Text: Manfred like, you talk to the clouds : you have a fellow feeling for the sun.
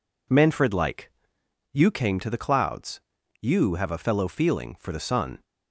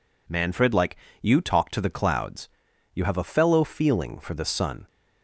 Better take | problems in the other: second | says "came" for "talk"; at 1.9 s

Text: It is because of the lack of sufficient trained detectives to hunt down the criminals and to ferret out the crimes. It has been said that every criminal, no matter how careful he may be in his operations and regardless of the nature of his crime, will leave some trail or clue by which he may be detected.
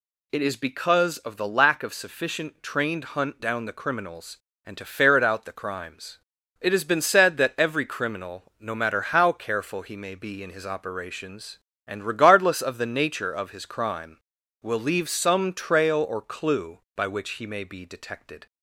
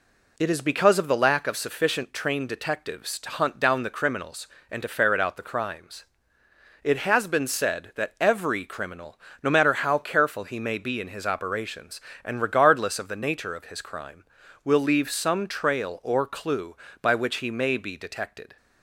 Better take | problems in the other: second | skips "detectives to"; at 3.1 s

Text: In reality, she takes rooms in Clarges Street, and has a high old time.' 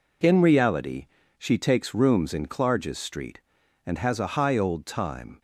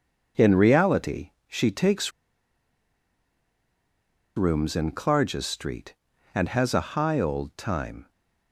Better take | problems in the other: first | pauses between "takes" and "rooms"; strong; at 2.1 s; 2.2 s long

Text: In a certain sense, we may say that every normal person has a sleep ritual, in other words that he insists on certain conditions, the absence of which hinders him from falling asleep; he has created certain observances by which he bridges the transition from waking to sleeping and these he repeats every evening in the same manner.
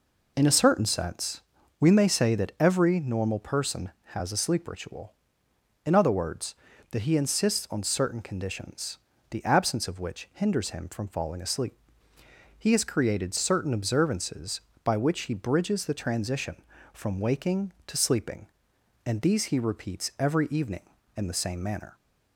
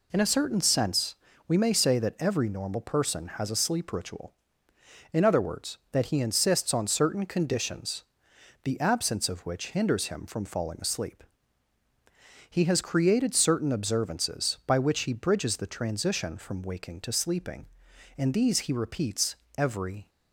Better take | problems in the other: first | pauses between "repeats" and "every"; slight; at 19.3 s; 0.20 s long // stops before "evening in the same manner"; at 20.0 s

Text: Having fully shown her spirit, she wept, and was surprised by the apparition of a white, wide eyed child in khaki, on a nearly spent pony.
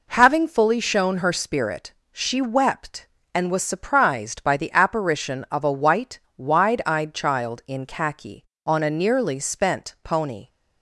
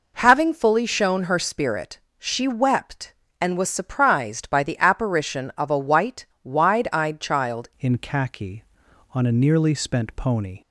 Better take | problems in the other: first | changes voice at "in"; from 7.7 s on; 2.9 s long

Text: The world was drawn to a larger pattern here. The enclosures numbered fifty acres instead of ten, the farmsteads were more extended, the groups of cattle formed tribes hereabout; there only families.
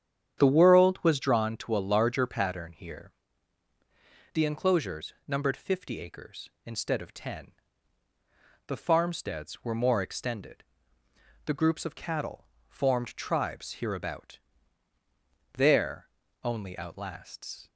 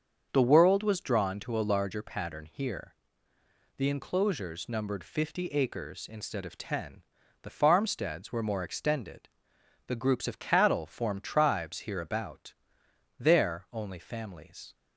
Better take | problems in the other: second | starts louder than the rest; strong; until 1.4 s; 9 dB; also in the second // pauses between "cattle" and "formed"; slight; at 12.4 s; 0.24 s long // pauses between "there" and "only"; at 16.0 s; 0.38 s long // says "outlasts" for "families"; at 16.7 s

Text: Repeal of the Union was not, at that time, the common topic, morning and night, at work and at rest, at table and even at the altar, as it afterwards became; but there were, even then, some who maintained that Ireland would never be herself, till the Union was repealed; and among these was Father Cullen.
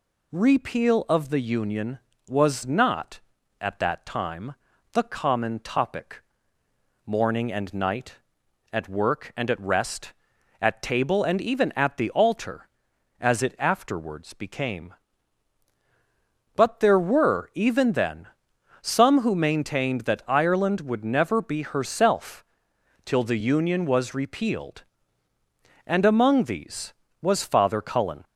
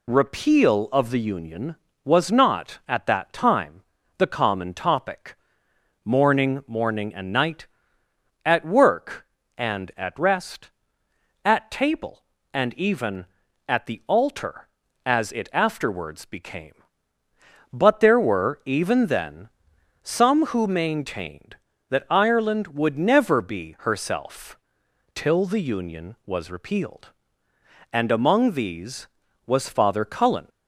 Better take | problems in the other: first | says "morning" twice; at 6.6 s

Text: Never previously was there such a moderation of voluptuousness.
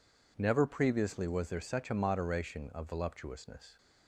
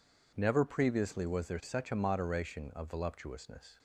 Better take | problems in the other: neither | none

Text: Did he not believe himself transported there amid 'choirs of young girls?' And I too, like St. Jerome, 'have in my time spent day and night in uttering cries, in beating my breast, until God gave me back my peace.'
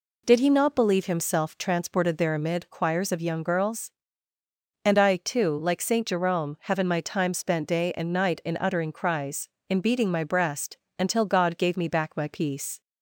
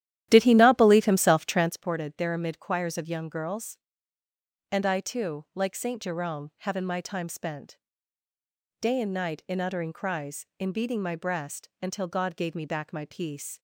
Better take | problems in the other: first | starts louder than the rest; strong; until 1.8 s; 12.5 dB // pauses between "spent" and "day"; at 7.7 s; 1.0 s long

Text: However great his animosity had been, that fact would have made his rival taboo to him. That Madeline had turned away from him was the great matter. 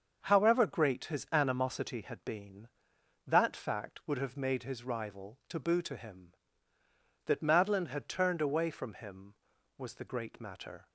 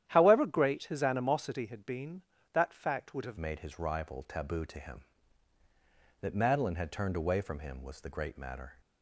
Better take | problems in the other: first | starts louder than the rest; strong; until 1.0 s; 11 dB; also in the first // changes voice at "made"; from 3.3 s on; 5.4 s long

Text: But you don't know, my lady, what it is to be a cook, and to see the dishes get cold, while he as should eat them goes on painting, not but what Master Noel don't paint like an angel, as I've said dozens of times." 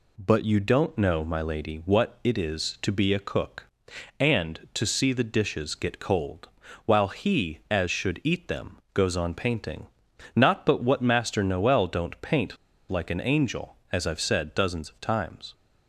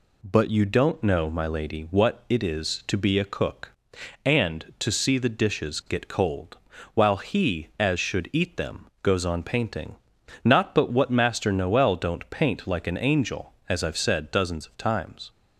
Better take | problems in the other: second | pauses between "them" and "goes"; slight; at 8.7 s; 0.16 s long; slight in the second // pauses between "paint" and "like"; slight; at 12.5 s; 0.32 s long

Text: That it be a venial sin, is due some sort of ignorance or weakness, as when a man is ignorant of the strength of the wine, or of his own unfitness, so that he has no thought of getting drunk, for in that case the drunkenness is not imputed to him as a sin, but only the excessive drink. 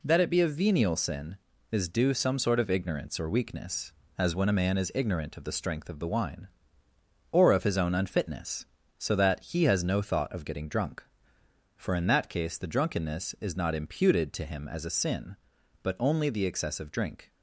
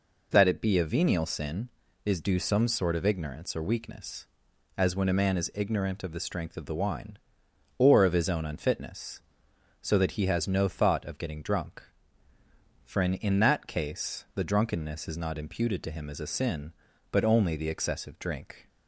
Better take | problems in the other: first | says "in" twice; at 13.1 s

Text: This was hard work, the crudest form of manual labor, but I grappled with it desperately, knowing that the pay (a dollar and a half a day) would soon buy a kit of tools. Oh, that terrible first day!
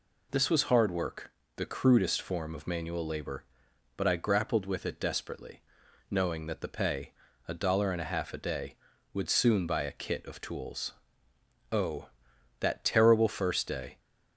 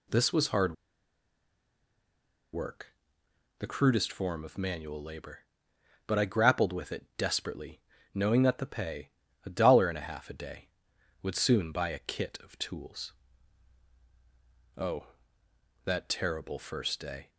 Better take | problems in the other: first | pauses between "hard" and "work"; strong; at 0.7 s; 1.8 s long

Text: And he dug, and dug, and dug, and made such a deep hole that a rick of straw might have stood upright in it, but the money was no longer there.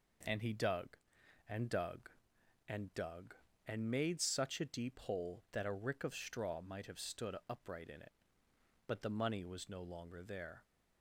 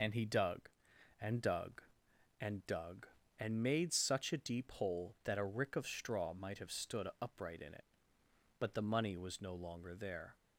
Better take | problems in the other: first | loses the start of "And"; at 0.0 s; 75 ms

